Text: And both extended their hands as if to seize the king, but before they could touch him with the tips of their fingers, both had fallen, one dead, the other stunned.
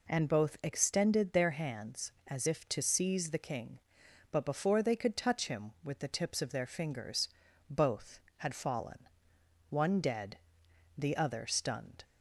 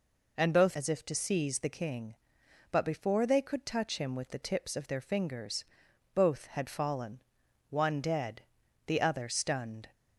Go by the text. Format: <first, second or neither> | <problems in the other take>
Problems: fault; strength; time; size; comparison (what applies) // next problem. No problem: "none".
first | skips "extended their hands"; at 0.7 s